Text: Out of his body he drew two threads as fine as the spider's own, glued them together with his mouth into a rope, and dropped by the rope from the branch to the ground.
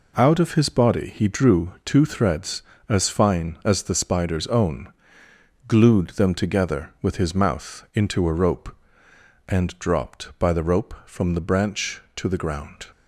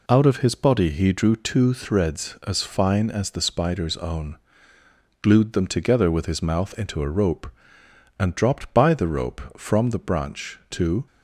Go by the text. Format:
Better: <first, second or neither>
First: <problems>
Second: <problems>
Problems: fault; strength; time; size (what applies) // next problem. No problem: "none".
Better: first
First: none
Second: stops before "the ground"; at 11.0 s